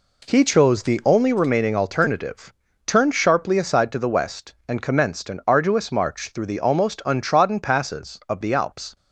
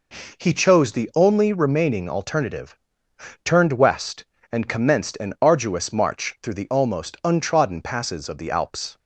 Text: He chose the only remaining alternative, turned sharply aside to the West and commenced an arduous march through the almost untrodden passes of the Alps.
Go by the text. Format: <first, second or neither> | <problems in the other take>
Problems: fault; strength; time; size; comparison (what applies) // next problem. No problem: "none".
first | skips "sharply aside to the"; at 3.7 s